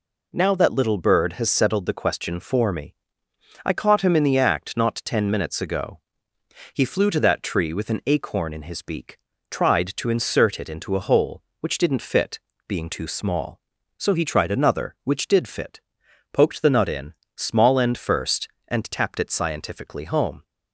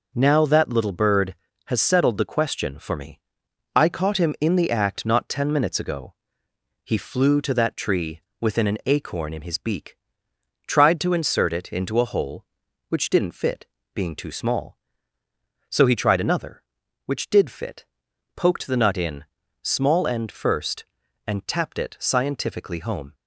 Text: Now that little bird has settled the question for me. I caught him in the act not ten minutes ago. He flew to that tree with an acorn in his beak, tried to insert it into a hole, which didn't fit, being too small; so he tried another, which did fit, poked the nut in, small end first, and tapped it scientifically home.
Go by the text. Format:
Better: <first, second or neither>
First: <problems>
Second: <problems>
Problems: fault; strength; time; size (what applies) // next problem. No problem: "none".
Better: first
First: none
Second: says "within" for "with"; at 8.3 s